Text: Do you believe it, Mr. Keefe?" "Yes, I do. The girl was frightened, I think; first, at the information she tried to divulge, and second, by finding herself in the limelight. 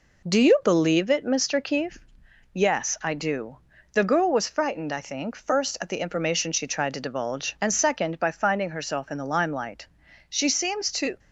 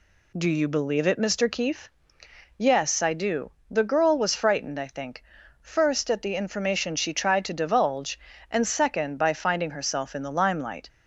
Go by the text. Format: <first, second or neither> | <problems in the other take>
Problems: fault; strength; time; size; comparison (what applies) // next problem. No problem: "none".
second | goes on to say "She seems to"; noticeable; from 10.2 s on; 0.90 s long